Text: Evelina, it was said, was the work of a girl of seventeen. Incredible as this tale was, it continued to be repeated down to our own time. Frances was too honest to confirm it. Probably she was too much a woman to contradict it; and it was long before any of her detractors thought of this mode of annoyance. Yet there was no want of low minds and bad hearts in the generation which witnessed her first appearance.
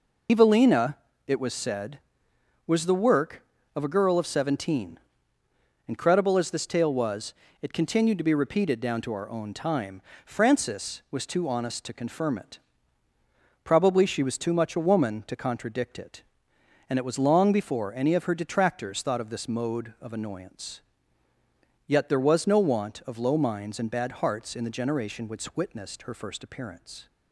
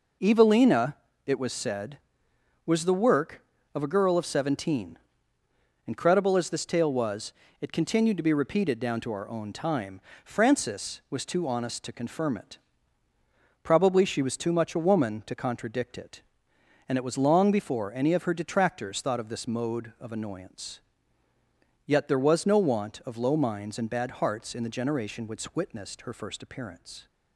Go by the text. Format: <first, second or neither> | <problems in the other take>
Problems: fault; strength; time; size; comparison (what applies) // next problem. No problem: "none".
second | loses the start of "Evelina"; at 0.2 s; 80 ms